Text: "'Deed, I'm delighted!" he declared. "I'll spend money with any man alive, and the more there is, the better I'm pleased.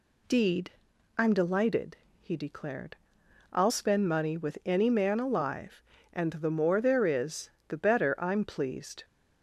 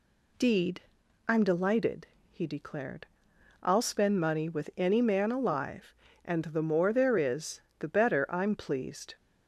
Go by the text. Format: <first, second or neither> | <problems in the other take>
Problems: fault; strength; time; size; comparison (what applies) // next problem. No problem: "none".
neither | none